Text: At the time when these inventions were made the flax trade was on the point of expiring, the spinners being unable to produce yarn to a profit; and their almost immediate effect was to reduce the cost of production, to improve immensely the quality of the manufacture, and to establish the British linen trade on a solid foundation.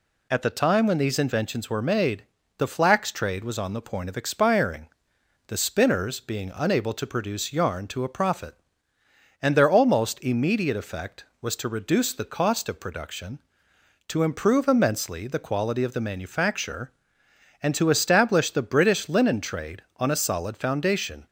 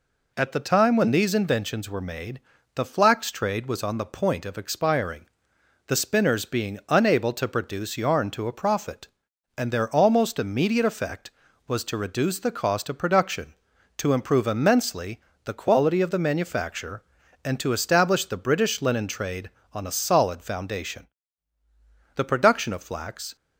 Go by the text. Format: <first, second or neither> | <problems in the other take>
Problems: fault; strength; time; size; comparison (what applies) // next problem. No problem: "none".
first | pauses between "made" and "the"; slight; at 2.3 s; 0.36 s long; slight in the first // pauses between "immensely" and "the"; slight; at 15.2 s; 0.22 s long // goes on to say "The production of flax"; noticeable; from 22.1 s on; 1.2 s long